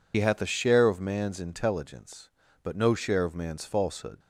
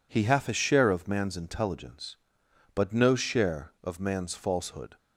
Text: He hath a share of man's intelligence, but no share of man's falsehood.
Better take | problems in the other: second | loses the start of "He"; at 0.1 s; 60 ms

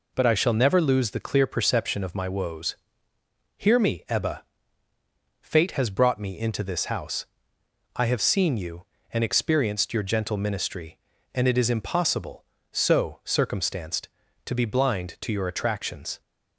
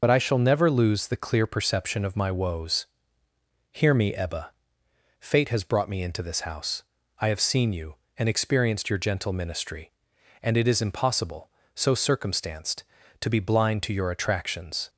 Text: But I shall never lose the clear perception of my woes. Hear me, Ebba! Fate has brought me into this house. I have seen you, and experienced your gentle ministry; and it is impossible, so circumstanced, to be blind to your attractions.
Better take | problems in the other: first | loses the start of "But"; at 0.0 s; 55 ms

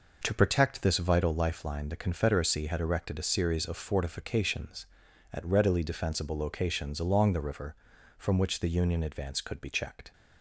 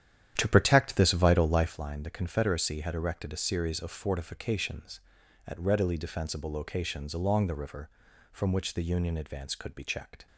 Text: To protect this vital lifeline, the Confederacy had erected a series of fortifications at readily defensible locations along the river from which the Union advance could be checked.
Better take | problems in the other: first | starts louder than the rest; strong; until 1.8 s; 10.5 dB

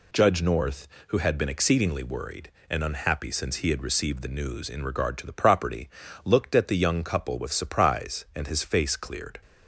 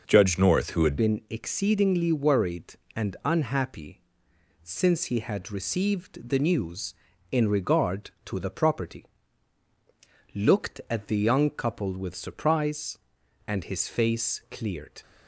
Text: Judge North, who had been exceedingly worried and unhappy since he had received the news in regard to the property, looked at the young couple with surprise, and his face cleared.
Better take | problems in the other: first | changes voice at "been"; from 0.9 s on; 14.1 s long // pauses between "unhappy" and "since"; noticeable; at 4.0 s; 0.62 s long

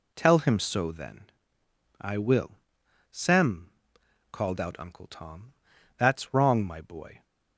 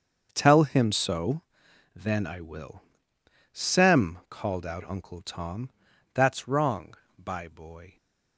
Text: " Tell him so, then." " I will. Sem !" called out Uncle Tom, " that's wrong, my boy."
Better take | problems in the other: first | starts louder than the rest; strong; until 1.3 s; 7.5 dB // says "by" for "my"; at 7.1 s

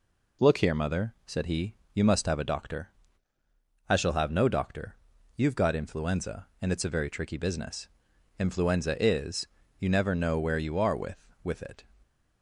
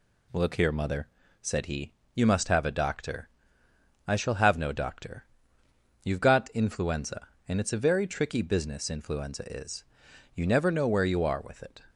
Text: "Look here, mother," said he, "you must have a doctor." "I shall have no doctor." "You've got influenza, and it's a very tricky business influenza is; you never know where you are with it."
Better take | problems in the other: second | pauses between "business" and "influenza"; noticeable; at 7.8 s; 0.48 s long // says "with" twice; at 11.4 s

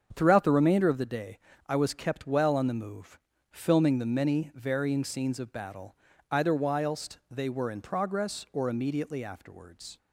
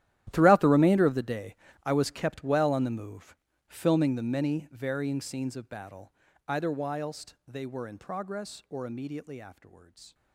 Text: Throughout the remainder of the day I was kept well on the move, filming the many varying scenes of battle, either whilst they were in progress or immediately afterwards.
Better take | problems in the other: first | gets quieter; strong; throughout; 19 dB // starts louder than the rest; strong; until 1.3 s; 13 dB; strong in the first // pauses between "day" and "I"; slight; at 1.5 s; 0.30 s long; slight in the first

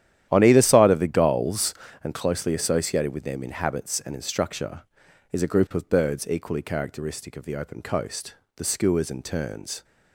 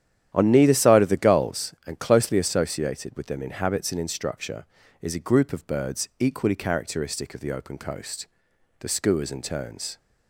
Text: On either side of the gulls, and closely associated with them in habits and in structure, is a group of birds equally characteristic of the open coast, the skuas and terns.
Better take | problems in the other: first | starts louder than the rest; strong; until 1.3 s; 10.5 dB; strong in the first // says "neither" for "either"; at 0.5 s

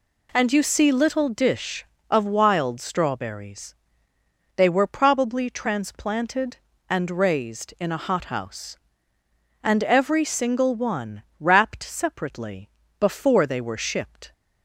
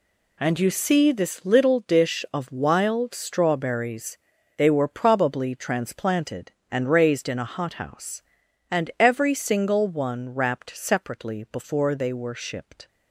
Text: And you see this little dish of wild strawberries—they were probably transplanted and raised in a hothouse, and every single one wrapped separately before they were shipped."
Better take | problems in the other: second | skips "this"; at 0.9 s // pauses between "one" and "wrapped"; slight; at 11.2 s; 0.16 s long // pauses between "separately" and "before"; slight; at 12.6 s; 0.30 s long

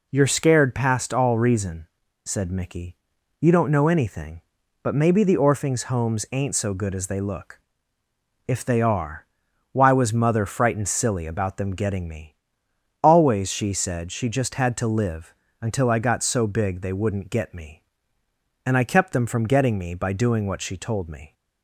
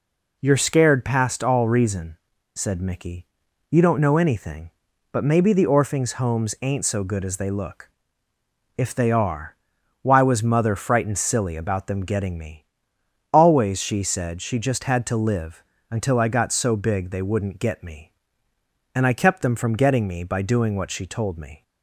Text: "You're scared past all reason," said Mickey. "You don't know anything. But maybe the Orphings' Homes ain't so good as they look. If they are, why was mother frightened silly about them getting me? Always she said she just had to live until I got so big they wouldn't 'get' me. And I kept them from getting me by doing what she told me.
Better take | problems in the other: neither | pauses between "live" and "until"; slight; the same in both

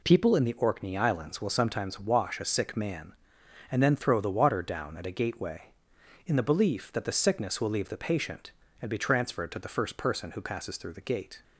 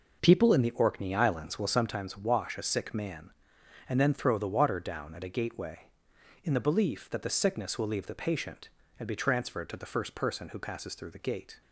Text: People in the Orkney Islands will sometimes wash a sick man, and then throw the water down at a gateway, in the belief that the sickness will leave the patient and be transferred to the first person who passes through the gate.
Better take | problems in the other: first | starts louder than the rest; noticeable; until 1.8 s; 5 dB

